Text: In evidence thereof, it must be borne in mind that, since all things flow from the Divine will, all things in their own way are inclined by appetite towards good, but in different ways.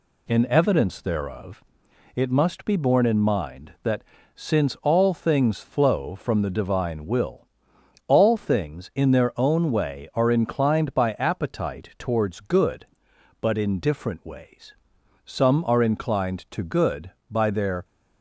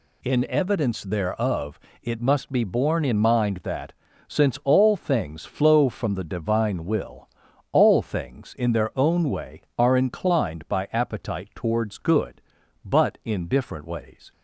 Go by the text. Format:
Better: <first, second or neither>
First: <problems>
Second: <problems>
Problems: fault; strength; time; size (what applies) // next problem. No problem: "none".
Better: second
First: goes on to say "Some are inclined to good by their"; strong; from 15.2 s on; 2.6 s long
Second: none